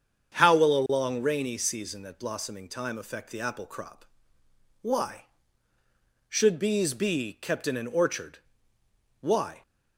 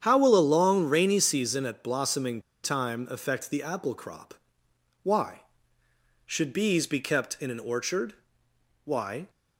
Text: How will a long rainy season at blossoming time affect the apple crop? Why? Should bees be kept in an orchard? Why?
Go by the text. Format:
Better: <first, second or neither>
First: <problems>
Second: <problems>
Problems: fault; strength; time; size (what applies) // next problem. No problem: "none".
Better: first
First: starts louder than the rest; strong; until 1.4 s; 7.5 dB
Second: starts louder than the rest; strong; until 1.0 s; 8.5 dB // pauses between "blossoming" and "time"; slight; at 2.4 s; 0.23 s long